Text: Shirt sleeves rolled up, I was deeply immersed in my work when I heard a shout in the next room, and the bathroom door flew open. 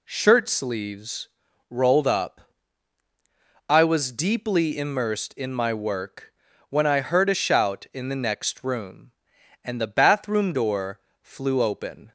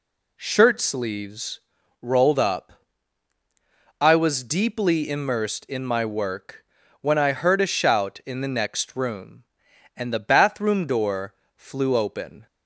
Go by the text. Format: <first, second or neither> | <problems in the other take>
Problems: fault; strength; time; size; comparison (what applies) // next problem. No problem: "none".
neither | pauses between "sleeves" and "rolled"; the same in both // pauses between "work" and "when"; the same in both // pauses between "door" and "flew"; slight; the same in both